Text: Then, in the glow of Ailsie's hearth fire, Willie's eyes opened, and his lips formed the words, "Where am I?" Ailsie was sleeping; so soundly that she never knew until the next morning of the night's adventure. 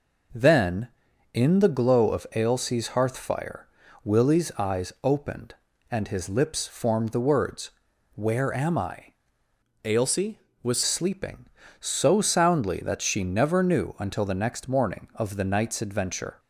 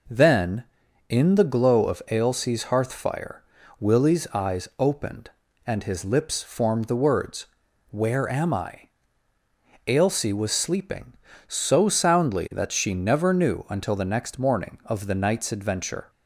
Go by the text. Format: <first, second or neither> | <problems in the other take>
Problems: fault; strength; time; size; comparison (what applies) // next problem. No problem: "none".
second | changes voice from "Ailsie" to "was"; from 9.8 to 10.8 s; 1.0 s long